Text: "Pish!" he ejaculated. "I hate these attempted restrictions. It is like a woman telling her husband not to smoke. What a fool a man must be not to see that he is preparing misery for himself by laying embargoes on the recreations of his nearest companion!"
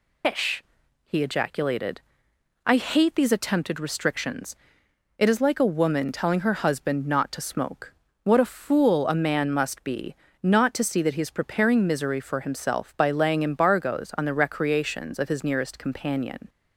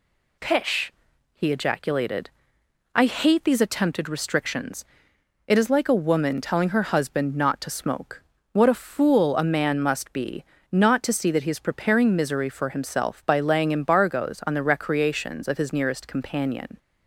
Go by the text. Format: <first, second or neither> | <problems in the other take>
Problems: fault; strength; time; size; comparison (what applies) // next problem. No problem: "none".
second | loses the start of "Pish"; at 0.2 s; 140 ms // pauses between "be" and "not"; slight; at 10.1 s; 0.26 s long; slight in the second